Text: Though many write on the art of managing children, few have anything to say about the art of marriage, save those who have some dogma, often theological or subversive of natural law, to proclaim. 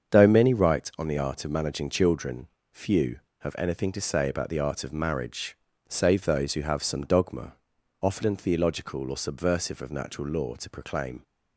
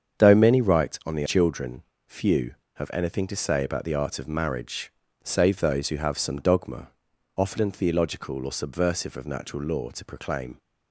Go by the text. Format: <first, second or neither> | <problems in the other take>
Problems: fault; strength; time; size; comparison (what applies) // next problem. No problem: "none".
first | starts louder than the rest; strong; until 1.2 s; 7.5 dB; strong in the first // skips "art of managing"; at 1.2 s